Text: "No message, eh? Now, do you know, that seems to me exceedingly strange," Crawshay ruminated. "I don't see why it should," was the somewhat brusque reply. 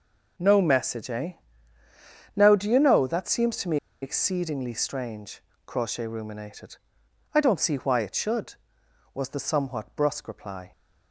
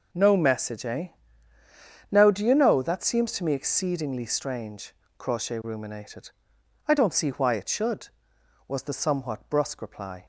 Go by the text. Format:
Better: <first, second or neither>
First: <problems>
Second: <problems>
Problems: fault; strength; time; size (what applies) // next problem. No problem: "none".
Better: second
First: pauses between "me" and "exceedingly"; slight; at 3.7 s; 0.25 s long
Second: none